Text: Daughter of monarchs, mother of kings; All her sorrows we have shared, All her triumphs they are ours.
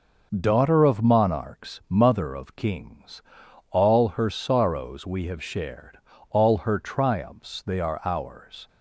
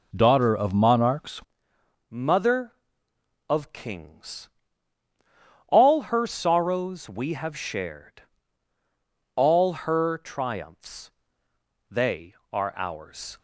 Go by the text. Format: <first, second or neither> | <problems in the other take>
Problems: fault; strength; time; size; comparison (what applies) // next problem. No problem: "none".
first | changes voice at "mother"; from 2.1 s on; 11.2 s long // pauses between "All" and "her"; slight; at 9.7 s; 0.16 s long // pauses between "triumphs" and "they"; noticeable; at 11.1 s; 0.80 s long